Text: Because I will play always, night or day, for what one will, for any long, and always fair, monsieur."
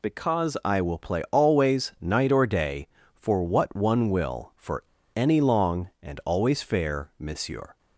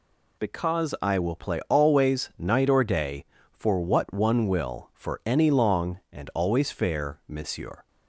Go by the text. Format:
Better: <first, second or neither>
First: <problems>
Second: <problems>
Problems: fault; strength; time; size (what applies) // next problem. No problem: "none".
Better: second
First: pauses between "for" and "any"; slight; at 4.8 s; 0.34 s long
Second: none